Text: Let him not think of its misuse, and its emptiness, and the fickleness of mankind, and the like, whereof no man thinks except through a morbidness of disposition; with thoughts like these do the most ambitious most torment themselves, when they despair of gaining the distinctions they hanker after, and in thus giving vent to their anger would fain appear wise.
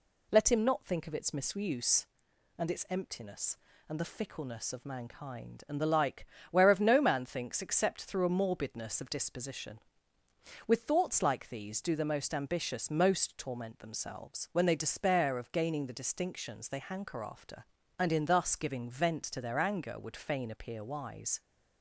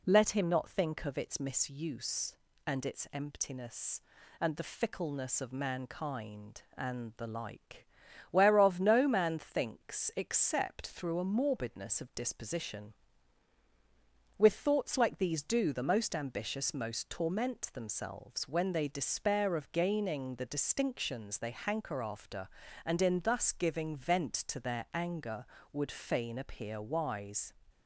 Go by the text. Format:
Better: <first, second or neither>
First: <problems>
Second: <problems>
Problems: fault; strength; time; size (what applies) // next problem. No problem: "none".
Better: neither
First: none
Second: none